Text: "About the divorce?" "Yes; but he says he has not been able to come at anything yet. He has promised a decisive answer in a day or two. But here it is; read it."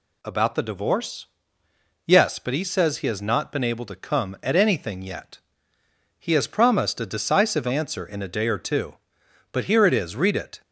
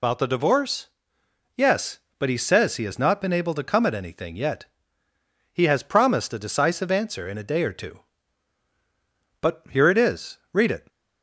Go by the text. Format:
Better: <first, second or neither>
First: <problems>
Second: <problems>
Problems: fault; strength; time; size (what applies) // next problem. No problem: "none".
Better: first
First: none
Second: loses the start of "About"; at 0.0 s; 145 ms